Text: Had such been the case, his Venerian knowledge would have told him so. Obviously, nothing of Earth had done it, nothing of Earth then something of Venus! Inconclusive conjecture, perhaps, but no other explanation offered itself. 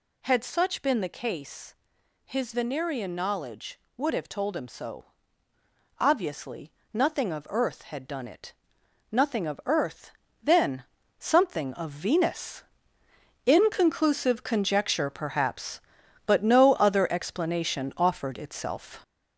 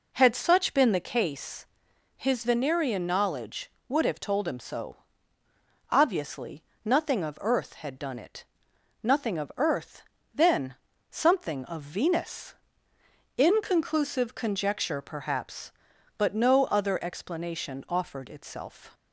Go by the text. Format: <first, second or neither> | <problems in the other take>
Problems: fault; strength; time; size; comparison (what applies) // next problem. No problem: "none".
second | gets louder; noticeable; throughout; 5 dB // pauses between "Earth" and "then"; slight; at 10.1 s; 0.32 s long; slight in the second // pauses between "then" and "something"; slight; at 10.8 s; 0.34 s long; slight in the second